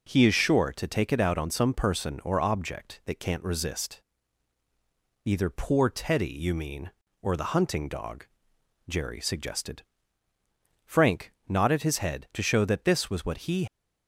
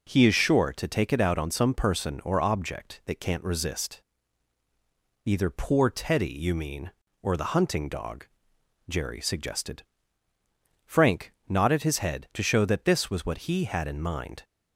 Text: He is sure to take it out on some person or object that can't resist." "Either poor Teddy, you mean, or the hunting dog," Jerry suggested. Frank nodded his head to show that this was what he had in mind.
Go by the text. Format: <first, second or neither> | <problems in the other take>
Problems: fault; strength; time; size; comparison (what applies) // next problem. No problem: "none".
second | stops before "had in mind"; at 13.6 s